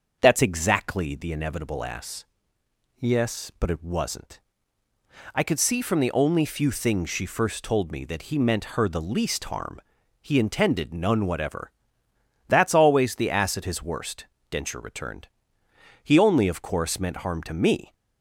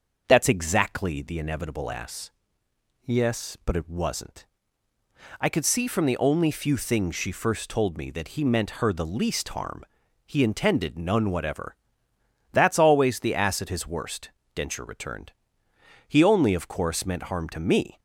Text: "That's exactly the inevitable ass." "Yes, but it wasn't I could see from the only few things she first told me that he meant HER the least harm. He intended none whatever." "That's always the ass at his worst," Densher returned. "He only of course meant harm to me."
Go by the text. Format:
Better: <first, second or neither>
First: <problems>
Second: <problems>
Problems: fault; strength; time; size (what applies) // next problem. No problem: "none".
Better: neither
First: starts louder than the rest; until 1.2 s; 6.5 dB // pauses between "wasn't" and "I"; noticeable; at 4.4 s; 0.94 s long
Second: starts louder than the rest; until 1.2 s; 6.5 dB // pauses between "wasn't" and "I"; noticeable; at 4.4 s; 0.94 s long